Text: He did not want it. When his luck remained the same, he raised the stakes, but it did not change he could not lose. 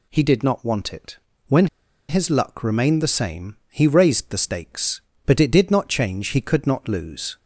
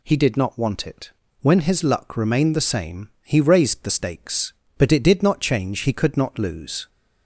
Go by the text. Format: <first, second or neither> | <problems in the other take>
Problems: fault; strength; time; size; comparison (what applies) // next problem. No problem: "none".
second | pauses between "When" and "his"; at 1.6 s; 0.42 s long